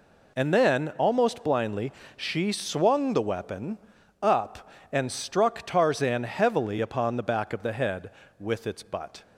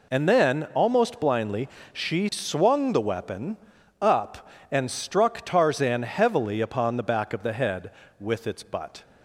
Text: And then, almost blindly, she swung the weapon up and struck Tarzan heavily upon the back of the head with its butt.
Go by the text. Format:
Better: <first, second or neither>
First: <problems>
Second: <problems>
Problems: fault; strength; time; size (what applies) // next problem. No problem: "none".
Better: neither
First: pauses between "weapon" and "up"; at 3.7 s; 0.44 s long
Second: pauses between "weapon" and "up"; at 3.5 s; 0.44 s long